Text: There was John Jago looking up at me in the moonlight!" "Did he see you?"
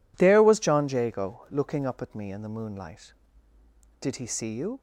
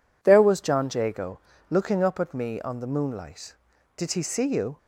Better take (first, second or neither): first